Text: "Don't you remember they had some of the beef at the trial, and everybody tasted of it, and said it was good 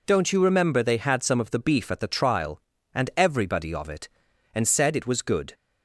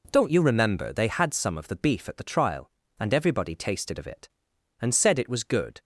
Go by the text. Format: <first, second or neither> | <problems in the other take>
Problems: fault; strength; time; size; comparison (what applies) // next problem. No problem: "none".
second | skips "tasted"; at 3.7 s